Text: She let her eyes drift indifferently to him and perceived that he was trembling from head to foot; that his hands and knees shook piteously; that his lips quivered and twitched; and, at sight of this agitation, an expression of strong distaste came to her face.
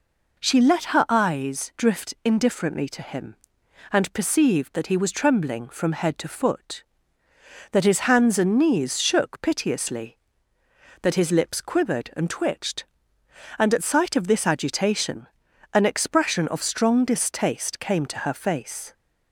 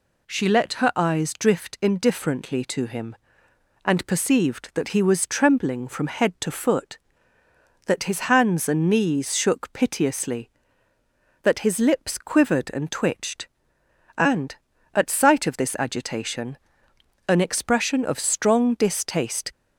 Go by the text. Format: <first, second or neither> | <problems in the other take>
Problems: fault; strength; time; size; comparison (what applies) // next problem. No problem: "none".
first | stops before "came to her face"; at 19.5 s